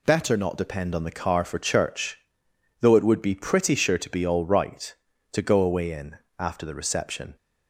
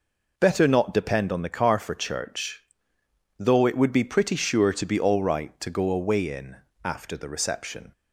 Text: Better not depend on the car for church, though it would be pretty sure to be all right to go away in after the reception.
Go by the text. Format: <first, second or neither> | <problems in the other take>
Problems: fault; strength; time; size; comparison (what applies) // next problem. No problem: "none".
neither | pauses between "in" and "after"; slight; the same in both